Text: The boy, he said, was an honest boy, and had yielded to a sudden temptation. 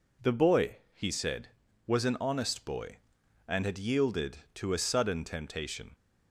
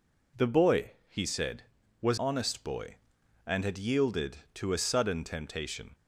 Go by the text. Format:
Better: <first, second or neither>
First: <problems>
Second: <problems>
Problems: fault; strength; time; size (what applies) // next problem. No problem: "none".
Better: first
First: none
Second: skips "an"; at 2.1 s